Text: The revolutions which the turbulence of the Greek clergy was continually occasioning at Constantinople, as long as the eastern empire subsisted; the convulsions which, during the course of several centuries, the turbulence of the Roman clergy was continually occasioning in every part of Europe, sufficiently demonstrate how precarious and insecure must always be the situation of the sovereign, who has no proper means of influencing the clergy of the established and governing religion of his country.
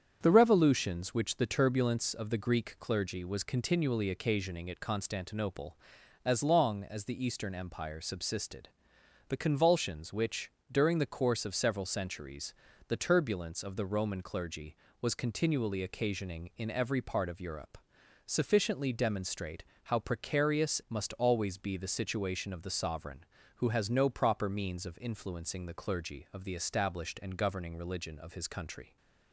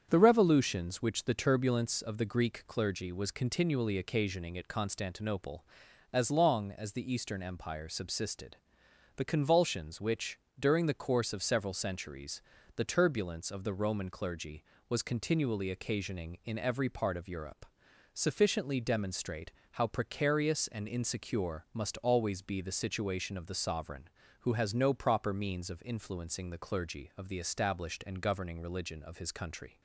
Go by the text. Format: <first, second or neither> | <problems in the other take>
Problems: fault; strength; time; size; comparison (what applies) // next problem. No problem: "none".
second | starts louder than the rest; strong; until 1.2 s; 8 dB; strong in the second // pauses between "demonstrate" and "how"; slight; at 19.6 s; 0.22 s long; slight in the second // skips "and insecure"; at 20.8 s